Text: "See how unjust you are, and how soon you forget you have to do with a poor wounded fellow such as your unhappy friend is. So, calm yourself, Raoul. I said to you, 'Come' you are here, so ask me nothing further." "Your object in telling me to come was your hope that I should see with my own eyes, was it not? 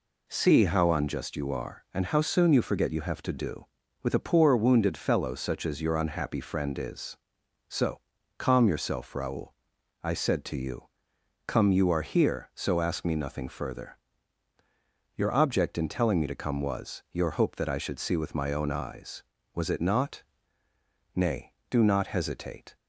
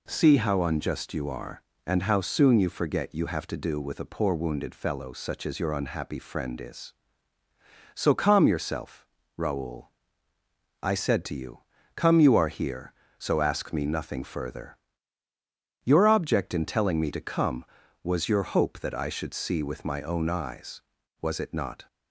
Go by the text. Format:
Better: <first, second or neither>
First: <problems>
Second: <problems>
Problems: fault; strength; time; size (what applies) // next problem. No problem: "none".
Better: second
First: goes on to say "Nay do not hesitate"; from 21.1 s on; 1.6 s long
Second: none